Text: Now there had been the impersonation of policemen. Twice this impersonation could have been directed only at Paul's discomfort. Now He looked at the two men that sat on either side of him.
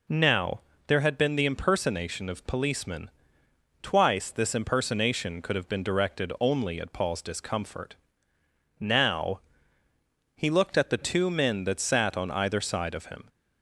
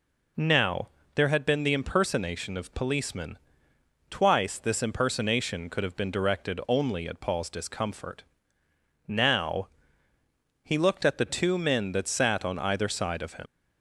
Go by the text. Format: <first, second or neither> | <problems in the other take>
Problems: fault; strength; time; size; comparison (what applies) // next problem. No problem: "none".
first | pauses between "Now" and "there"; slight; at 0.8 s; 0.26 s long; slight in the first // pauses between "Now" and "He"; noticeable; at 9.6 s; 0.94 s long; noticeable in the first // leaves "him" unfinished; at 13.4 s; 100 ms